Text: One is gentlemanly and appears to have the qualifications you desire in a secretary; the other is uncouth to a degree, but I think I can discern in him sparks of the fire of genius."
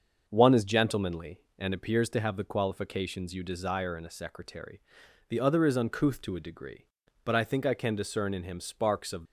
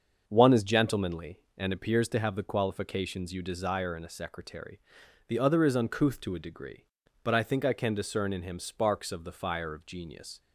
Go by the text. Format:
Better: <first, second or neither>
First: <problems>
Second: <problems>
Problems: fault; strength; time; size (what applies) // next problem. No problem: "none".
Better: second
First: starts louder than the rest; until 1.2 s; 6.5 dB // stops before "the fire of genius"; at 9.2 s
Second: starts louder than the rest; until 1.2 s; 7 dB